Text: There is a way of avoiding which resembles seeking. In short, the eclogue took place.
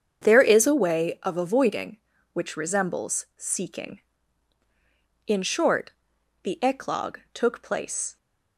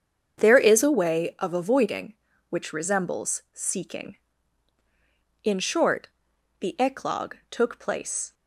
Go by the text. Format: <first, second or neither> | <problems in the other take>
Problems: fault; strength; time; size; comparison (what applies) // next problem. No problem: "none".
neither | starts louder than the rest; strong; the same in both